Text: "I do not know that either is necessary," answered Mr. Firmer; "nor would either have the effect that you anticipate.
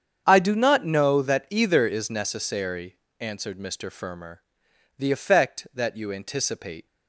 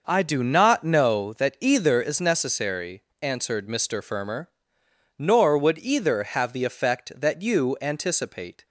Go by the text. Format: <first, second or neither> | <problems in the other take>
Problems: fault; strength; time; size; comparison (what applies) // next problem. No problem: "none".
second | starts louder than the rest; strong; until 1.2 s; 8 dB; noticeable in the second // skips "nor would either have"; at 4.6 s